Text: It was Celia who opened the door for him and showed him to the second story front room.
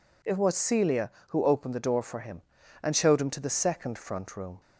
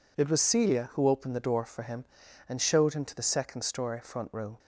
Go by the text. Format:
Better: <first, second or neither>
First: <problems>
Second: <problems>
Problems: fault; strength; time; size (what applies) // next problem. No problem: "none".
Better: second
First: skips "story"; at 3.9 s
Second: none